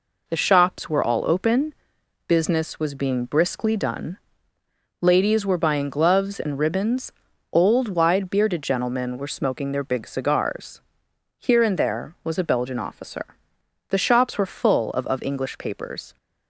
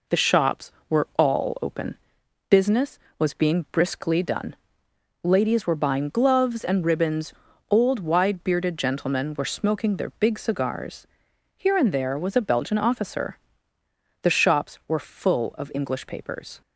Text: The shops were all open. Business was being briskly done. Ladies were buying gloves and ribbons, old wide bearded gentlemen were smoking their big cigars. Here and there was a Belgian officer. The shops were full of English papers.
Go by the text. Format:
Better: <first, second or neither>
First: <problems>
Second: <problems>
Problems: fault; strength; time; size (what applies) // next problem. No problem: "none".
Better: second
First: says "of" twice; at 15.0 s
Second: none